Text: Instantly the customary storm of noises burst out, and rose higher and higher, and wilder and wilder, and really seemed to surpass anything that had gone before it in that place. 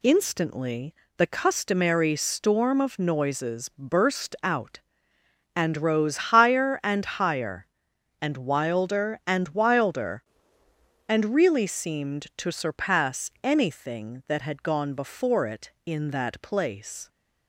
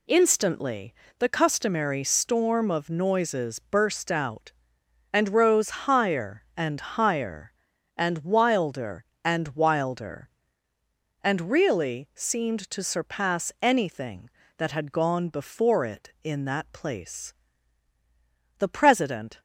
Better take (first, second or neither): first